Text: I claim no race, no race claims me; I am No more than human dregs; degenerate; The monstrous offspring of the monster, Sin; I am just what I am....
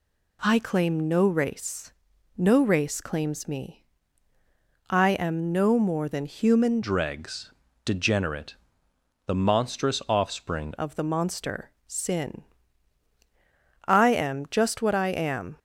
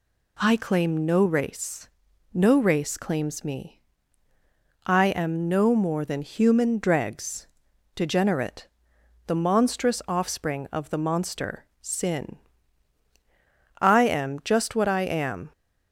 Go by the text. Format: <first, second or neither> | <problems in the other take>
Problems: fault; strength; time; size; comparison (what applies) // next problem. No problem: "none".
second | changes voice from "dregs" to "offspring"; from 6.8 to 10.7 s; 3.9 s long